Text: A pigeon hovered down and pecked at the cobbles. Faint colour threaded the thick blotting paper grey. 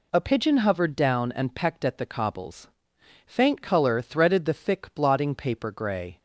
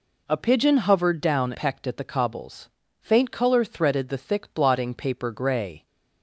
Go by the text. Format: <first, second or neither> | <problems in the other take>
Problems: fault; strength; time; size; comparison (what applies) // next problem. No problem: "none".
first | skips "and"; at 1.5 s